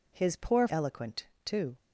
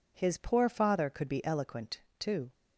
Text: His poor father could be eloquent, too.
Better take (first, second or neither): second